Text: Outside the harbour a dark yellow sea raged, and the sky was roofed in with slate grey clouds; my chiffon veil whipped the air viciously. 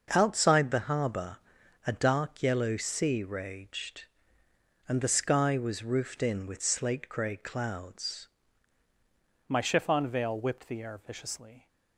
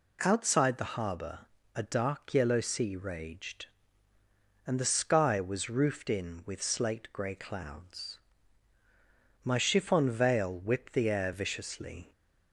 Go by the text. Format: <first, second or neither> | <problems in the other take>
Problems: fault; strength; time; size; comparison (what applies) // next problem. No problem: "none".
second | starts louder than the rest; until 1.1 s; 6 dB // pauses between "harbour" and "a"; noticeable; at 1.3 s; 0.48 s long; slight in the second // changes voice at "my"; from 9.4 s on; 2.2 s long